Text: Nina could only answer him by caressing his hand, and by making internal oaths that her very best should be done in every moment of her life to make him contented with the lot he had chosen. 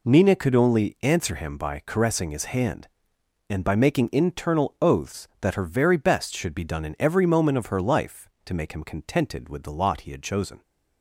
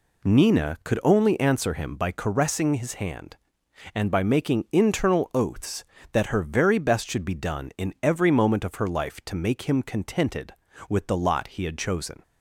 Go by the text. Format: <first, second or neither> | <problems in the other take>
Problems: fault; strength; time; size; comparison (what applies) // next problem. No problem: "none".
neither | none